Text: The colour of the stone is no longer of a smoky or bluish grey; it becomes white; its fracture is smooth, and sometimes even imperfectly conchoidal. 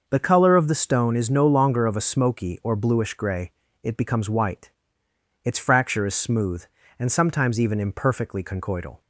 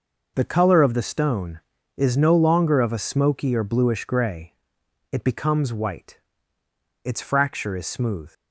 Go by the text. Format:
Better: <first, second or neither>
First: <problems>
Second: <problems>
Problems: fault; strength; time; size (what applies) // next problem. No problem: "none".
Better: first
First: none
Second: stops before "and sometimes even imperfectly conchoidal"; at 8.3 s